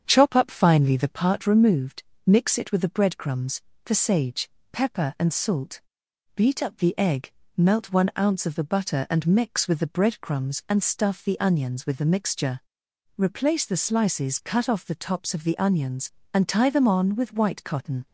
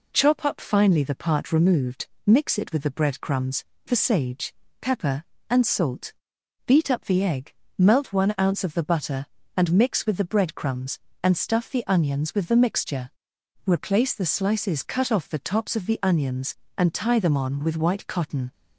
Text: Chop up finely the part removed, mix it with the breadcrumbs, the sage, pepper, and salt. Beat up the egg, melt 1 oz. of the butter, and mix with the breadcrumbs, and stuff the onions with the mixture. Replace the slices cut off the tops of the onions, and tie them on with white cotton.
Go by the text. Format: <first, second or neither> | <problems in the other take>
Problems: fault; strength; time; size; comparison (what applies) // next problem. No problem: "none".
second | starts louder than the rest; strong; until 1.2 s; 8 dB